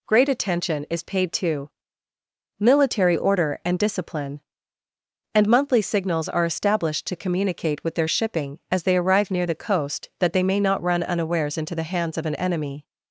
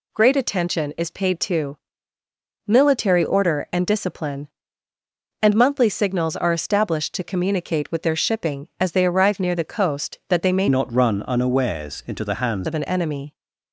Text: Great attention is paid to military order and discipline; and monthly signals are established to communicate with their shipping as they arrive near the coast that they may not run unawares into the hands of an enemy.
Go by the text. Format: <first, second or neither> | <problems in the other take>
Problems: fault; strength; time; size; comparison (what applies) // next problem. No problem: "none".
first | pauses between "to" and "military"; noticeable; at 1.7 s; 0.90 s long; noticeable in the first // changes voice from "not" to "hands"; from 10.6 to 12.6 s; 2.0 s long